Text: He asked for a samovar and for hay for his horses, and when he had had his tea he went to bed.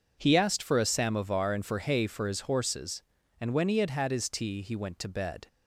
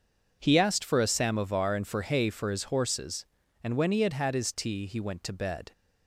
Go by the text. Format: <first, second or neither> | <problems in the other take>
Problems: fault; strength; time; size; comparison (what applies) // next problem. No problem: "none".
neither | none